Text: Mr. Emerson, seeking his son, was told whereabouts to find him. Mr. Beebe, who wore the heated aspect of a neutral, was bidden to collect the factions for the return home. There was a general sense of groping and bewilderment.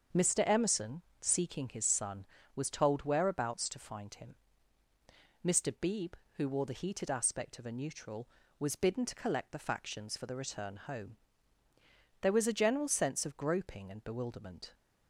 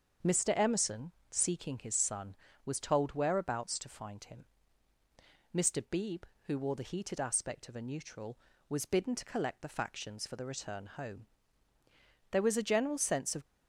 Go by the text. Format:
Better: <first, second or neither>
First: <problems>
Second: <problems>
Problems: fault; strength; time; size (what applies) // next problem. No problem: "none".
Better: first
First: starts louder than the rest; until 1.3 s; 7 dB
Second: starts louder than the rest; until 1.4 s; 7 dB // stops before "groping and bewilderment"; at 13.4 s